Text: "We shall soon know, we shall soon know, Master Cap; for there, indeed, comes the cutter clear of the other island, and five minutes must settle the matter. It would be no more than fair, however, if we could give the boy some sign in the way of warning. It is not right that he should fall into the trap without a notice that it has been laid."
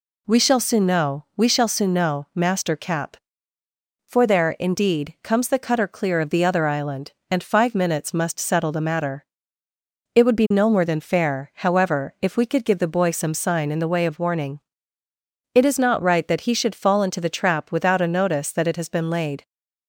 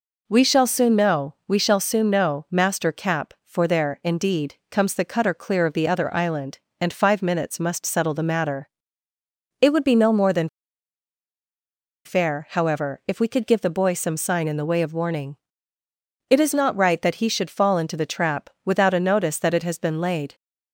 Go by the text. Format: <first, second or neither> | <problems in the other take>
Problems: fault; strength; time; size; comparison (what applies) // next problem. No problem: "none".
first | pauses between "than" and "fair"; strong; at 10.4 s; 1.5 s long